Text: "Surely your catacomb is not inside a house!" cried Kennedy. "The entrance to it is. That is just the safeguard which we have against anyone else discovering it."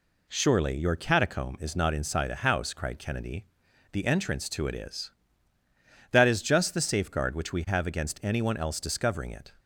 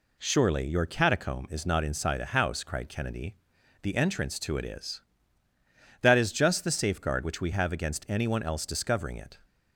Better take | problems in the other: neither | none

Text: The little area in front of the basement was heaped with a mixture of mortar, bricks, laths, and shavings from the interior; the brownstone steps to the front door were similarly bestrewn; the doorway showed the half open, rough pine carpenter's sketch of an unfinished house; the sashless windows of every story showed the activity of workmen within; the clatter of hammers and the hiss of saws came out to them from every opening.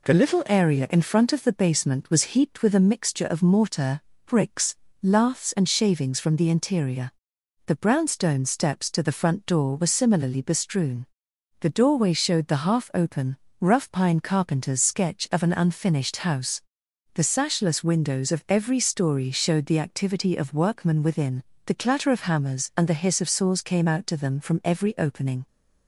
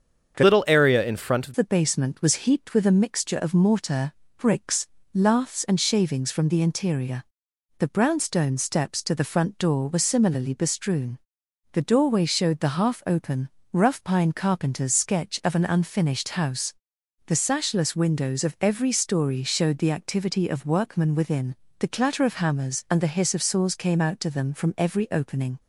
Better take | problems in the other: first | starts louder than the rest; strong; until 1.3 s; 7 dB // changes voice from "little" to "of"; from 0.4 to 1.5 s; 1.1 s long

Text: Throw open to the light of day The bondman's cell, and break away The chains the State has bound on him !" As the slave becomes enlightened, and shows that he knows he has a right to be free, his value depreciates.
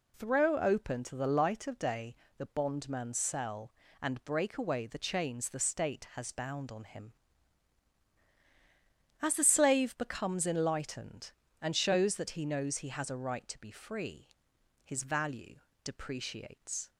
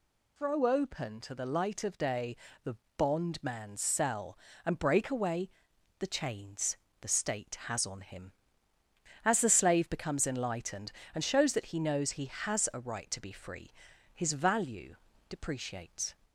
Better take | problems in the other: first | pauses between "day" and "The"; slight; at 2.3 s; 0.28 s long; slight in the first // pauses between "The" and "bondman's"; slight; at 2.7 s; 0.20 s long // pauses between "away" and "The"; noticeable; at 5.5 s; 0.50 s long // pauses between "chains" and "the"; slight; at 6.7 s; 0.26 s long // skips "bound"; at 7.8 s // pauses between "value" and "depreciates"; slight; at 14.9 s; 0.32 s long; slight in the first

